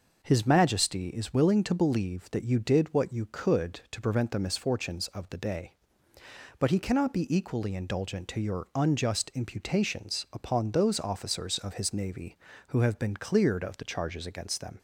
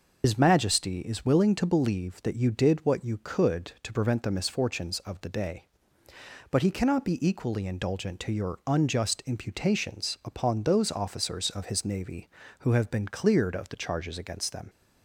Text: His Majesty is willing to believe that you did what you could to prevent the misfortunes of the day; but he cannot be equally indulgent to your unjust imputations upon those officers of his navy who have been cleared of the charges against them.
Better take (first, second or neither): first